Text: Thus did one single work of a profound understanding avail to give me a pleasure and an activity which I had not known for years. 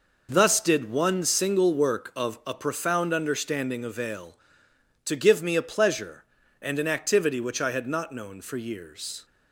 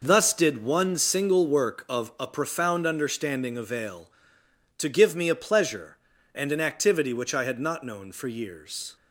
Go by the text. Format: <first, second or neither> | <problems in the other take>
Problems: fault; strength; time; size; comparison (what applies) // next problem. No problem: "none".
neither | none